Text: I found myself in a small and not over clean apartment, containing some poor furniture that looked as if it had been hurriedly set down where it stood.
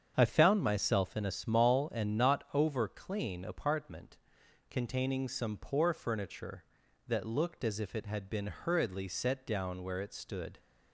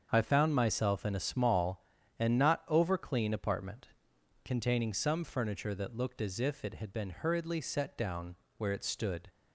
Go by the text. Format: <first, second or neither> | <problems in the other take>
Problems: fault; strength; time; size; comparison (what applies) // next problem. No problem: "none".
first | starts louder than the rest; until 1.1 s; 7 dB; strong in the first // skips "poor"; at 5.2 s // pauses between "down" and "where"; slight; at 8.3 s; 0.24 s long